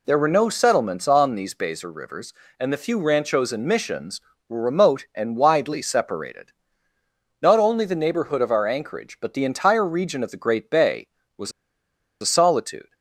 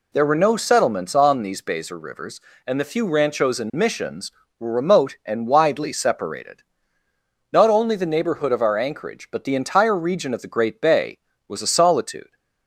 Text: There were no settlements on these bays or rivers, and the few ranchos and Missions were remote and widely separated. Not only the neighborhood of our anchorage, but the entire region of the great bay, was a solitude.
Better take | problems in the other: second | pauses between "was" and "a"; noticeable; at 11.5 s; 0.69 s long

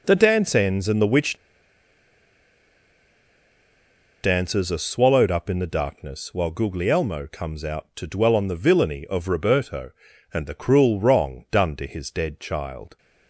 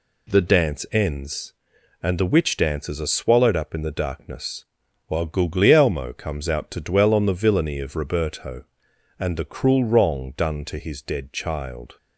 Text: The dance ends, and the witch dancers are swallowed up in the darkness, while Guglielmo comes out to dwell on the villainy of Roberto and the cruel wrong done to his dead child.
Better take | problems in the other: second | pauses between "witch" and "dancers"; strong; at 1.3 s; 2.8 s long

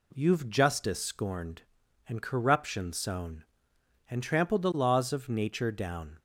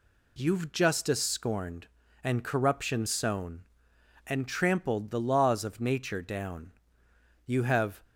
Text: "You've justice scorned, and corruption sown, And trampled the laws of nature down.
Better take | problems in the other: first | goes on to say "You have"; from 7.4 s on; 0.56 s long

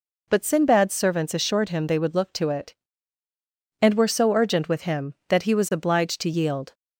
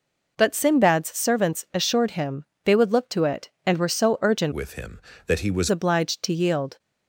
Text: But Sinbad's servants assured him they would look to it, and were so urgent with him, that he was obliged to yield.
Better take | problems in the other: first | pauses between "him" and "they"; slight; at 2.4 s; 0.20 s long // changes voice from "with" to "was"; from 4.5 to 5.6 s; 1.1 s long

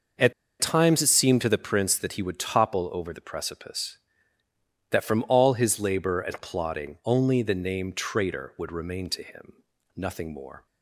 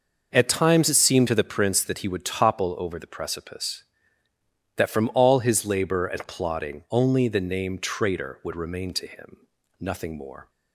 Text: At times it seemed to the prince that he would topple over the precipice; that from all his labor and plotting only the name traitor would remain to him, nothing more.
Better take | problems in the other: second | pauses between "At" and "times"; slight; at 0.3 s; 0.26 s long

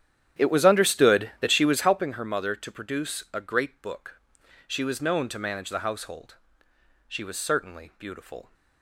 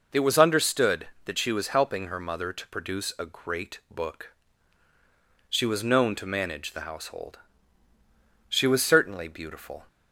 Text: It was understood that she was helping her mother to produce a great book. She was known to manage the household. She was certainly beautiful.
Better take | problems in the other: second | starts louder than the rest; strong; until 2.1 s; 10 dB

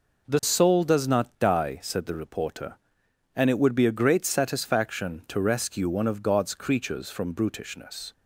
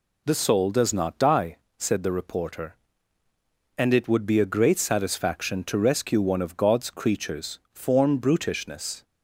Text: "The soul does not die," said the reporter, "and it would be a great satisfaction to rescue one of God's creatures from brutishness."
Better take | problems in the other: first | says "form" for "from"; at 7.7 s

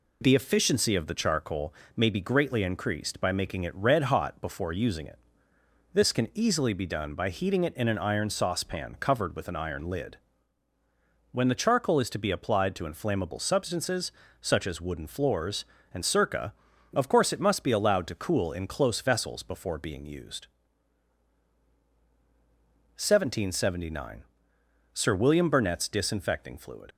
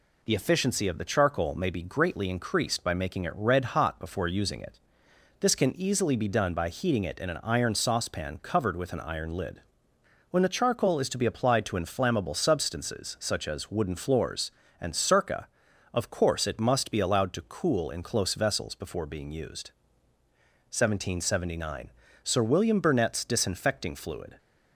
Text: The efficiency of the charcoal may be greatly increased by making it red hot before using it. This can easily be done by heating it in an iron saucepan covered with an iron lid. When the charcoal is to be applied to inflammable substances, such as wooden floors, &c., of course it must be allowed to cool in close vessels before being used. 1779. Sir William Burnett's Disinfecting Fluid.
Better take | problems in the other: second | pauses between "charcoal" and "may"; slight; at 1.7 s; 0.22 s long // leaves "Fluid" unfinished; at 26.9 s; 55 ms

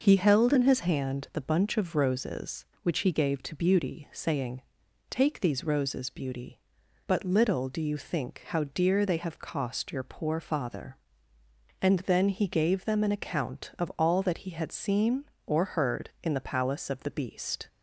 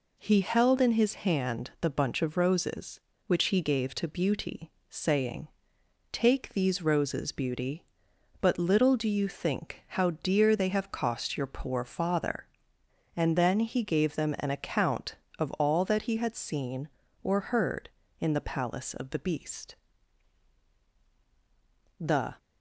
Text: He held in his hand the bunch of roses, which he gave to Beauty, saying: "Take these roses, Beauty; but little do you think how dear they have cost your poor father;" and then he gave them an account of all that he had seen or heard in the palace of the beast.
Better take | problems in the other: first | goes on to say "The"; slight; from 22.0 s on; 0.34 s long

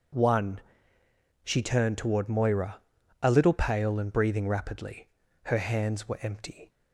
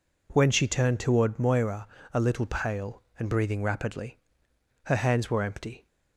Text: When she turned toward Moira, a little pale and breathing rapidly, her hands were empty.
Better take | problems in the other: second | says "One" for "When"; at 0.1 s

